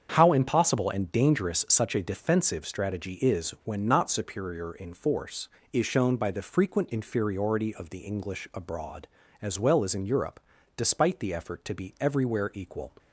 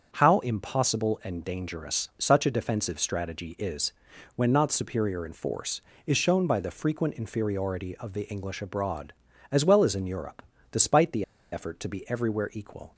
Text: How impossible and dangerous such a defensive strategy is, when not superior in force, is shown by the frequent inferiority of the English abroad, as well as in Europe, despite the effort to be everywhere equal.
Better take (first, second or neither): first